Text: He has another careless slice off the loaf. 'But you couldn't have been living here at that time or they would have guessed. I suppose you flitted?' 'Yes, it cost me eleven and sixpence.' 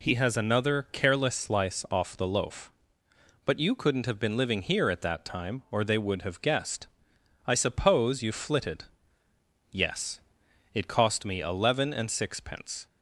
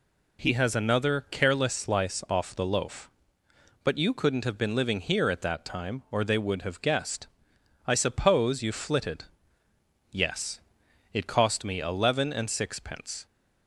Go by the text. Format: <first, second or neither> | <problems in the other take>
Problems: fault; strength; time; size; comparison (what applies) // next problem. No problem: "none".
neither | none